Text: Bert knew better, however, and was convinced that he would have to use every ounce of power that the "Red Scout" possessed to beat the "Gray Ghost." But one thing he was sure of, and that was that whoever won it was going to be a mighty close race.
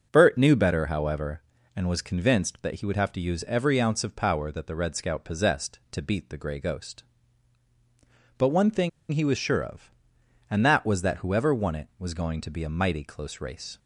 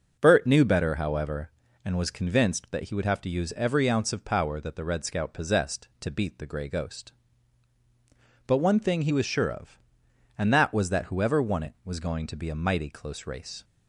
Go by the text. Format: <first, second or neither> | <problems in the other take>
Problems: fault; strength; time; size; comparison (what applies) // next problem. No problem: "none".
second | pauses between "thing" and "he"; slight; at 8.8 s; 0.22 s long